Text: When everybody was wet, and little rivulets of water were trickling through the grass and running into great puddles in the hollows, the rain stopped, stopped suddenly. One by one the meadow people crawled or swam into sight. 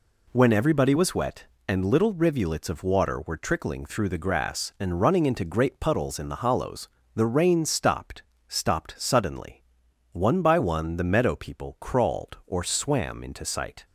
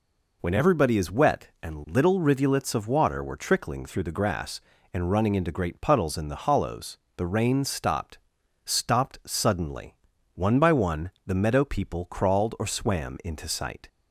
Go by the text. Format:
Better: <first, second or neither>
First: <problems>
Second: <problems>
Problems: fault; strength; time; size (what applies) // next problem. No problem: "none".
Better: first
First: none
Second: says "is" for "was"; at 0.9 s